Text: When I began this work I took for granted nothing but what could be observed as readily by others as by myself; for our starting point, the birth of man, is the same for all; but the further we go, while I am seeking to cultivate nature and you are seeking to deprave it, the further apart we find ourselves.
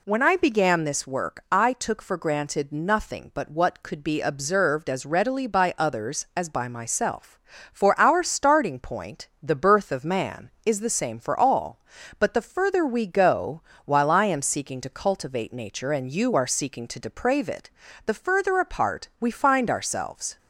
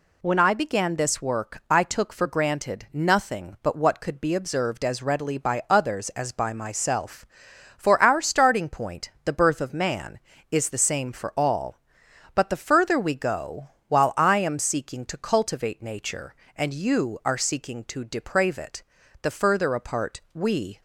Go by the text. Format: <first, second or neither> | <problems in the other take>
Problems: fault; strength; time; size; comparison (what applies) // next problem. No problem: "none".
first | pauses between "apart" and "we"; slight; at 20.1 s; 0.16 s long // stops before "find ourselves"; at 20.7 s